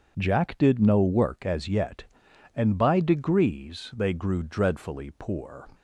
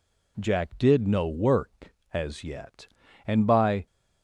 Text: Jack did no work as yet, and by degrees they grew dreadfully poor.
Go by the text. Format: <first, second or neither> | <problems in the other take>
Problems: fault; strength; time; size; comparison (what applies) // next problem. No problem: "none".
first | stops before "degrees they grew dreadfully poor"; at 3.8 s